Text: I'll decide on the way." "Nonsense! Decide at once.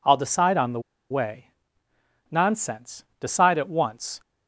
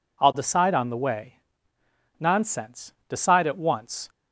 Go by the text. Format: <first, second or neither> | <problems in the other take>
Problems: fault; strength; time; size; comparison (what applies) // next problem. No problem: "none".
second | pauses between "the" and "way"; slight; at 0.8 s; 0.30 s long